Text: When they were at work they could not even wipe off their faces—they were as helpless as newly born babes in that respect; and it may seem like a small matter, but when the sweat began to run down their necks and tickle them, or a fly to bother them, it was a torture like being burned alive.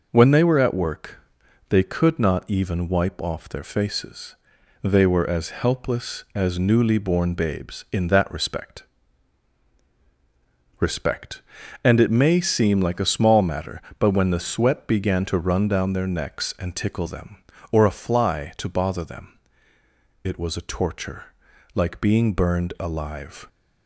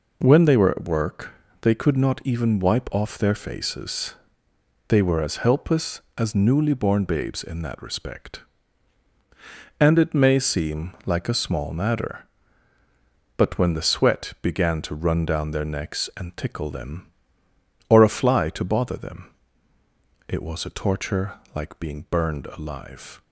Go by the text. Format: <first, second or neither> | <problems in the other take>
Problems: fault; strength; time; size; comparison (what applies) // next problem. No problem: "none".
second | pauses between "work" and "they"; noticeable; at 1.1 s; 0.50 s long; slight in the second // says "respect" twice; at 10.7 s // pauses between "torture" and "like"; at 21.3 s; 0.40 s long; slight in the second